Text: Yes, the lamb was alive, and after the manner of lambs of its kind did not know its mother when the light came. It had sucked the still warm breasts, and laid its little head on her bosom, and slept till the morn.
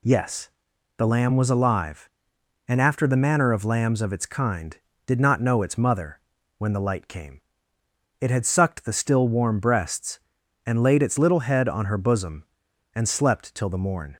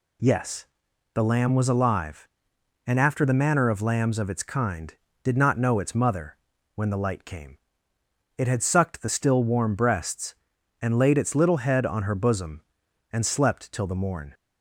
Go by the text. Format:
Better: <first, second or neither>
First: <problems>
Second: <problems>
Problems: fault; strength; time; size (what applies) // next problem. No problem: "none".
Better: neither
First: pauses between "mother" and "when"; at 6.1 s; 0.40 s long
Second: pauses between "mother" and "when"; at 6.3 s; 0.40 s long